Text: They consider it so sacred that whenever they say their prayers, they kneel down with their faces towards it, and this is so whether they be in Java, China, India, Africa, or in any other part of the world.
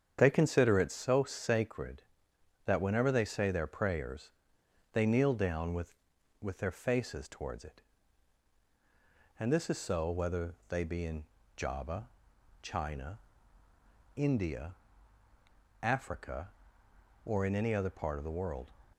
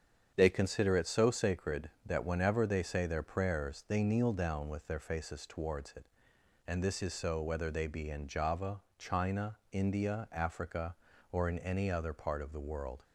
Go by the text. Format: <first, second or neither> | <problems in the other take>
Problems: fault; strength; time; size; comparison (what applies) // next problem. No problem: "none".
second | starts louder than the rest; strong; until 1.2 s; 8 dB; strong in the second // says "with" twice; at 6.4 s // pauses between "in" and "Java"; slight; at 11.2 s; 0.32 s long